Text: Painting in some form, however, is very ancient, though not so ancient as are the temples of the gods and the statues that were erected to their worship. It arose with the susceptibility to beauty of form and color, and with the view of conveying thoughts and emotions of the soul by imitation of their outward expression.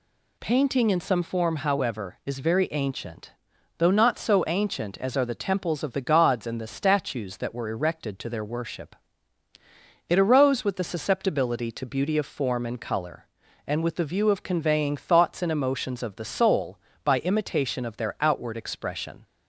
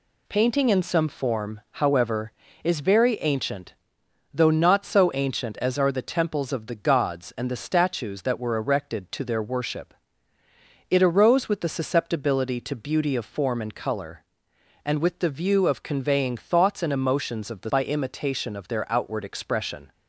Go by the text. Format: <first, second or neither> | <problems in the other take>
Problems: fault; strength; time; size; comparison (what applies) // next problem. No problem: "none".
first | skips "soul"; at 17.6 s